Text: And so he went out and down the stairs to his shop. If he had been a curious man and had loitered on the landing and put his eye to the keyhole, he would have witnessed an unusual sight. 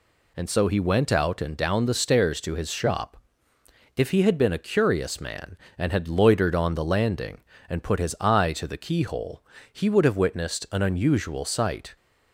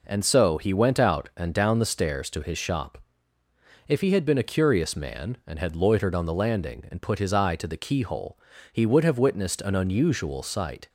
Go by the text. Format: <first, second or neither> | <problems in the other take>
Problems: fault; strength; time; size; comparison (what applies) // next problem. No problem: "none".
neither | none